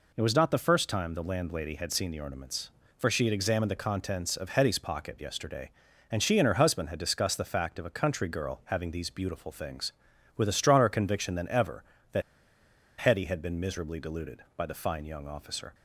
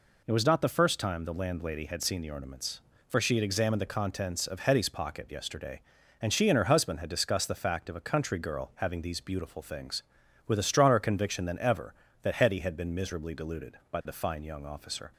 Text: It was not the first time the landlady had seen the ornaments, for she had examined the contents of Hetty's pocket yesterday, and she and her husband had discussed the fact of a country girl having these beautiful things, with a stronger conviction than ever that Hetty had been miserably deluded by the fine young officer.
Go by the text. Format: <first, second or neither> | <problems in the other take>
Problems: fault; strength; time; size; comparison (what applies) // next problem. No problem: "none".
second | pauses between "that" and "Hetty"; noticeable; at 12.2 s; 0.77 s long